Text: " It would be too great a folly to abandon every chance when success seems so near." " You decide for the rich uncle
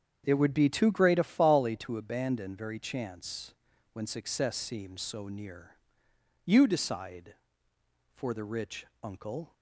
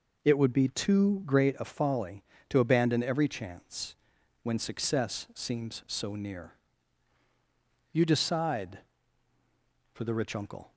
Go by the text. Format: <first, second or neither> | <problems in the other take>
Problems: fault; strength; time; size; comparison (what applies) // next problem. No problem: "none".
second | starts louder than the rest; strong; until 1.2 s; 8 dB // says "very" for "every"; at 2.5 s // pauses between "chance" and "when"; at 3.5 s; 0.40 s long; noticeable in the second // pauses between "rich" and "uncle"; slight; at 8.8 s; 0.16 s long